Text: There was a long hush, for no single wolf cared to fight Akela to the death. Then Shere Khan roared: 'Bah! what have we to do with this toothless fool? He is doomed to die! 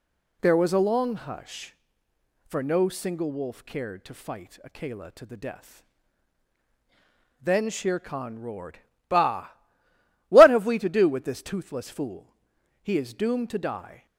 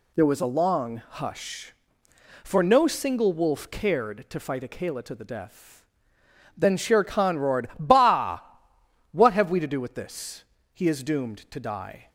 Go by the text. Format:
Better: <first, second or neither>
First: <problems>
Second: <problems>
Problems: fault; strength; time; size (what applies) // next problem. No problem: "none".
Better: first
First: none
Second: skips "toothless fool"; at 10.5 s